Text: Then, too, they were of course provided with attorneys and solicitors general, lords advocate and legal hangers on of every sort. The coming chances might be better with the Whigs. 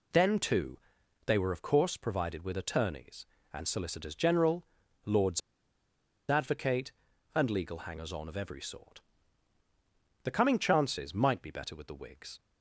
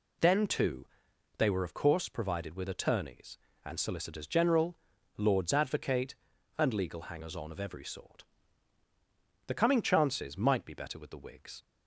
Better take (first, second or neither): second